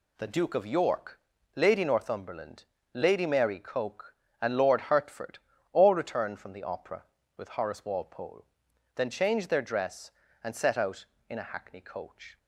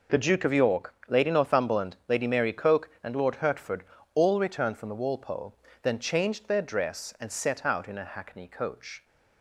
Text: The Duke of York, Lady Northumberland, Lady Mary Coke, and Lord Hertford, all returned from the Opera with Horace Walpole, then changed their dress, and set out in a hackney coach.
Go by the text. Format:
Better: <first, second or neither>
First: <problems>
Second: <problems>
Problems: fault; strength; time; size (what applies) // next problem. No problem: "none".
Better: first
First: none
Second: skips "Opera with Horace"; at 5.0 s